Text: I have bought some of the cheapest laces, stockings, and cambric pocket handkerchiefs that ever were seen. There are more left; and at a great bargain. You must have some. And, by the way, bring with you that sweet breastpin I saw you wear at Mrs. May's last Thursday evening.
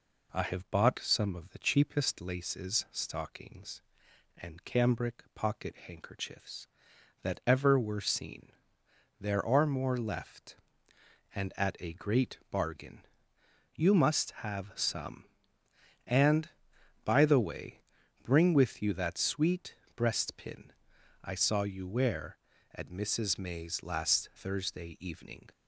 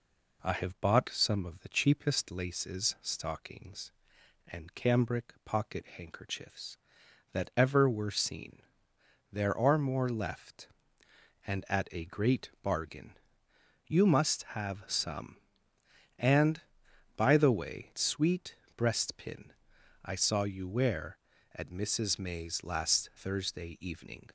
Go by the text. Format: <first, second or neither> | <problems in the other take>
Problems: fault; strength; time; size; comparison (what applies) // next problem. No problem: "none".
first | skips "bring with you that"; at 17.9 s // pauses between "sweet" and "breastpin"; slight; at 18.5 s; 0.22 s long; slight in the first // pauses between "breastpin" and "I"; noticeable; at 19.5 s; 0.54 s long; noticeable in the first